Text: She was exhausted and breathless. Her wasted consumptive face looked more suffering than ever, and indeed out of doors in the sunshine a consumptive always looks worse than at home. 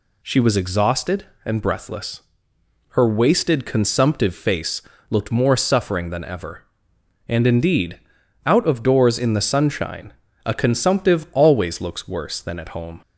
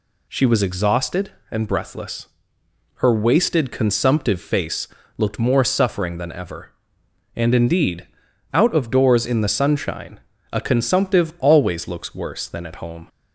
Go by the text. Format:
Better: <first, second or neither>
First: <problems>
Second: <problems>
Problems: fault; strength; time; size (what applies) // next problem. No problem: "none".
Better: neither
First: pauses between "face" and "looked"; slight; at 4.8 s; 0.28 s long // pauses between "indeed" and "out"; noticeable; at 7.9 s; 0.46 s long // pauses between "sunshine" and "a"; slight; at 10.1 s; 0.32 s long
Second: pauses between "face" and "looked"; slight; at 4.8 s; 0.30 s long // pauses between "indeed" and "out"; noticeable; at 8.0 s; 0.46 s long // pauses between "sunshine" and "a"; slight; at 10.2 s; 0.32 s long